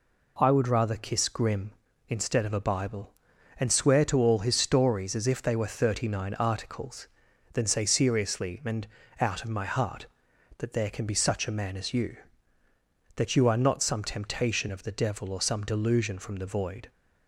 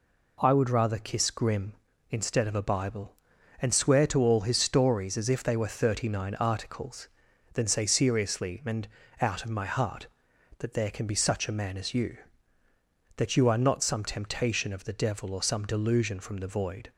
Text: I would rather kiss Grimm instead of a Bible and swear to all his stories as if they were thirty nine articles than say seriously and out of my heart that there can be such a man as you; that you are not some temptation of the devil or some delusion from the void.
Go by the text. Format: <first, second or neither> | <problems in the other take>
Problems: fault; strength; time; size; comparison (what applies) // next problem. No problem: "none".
neither | pauses between "and" and "out"; slight; the same in both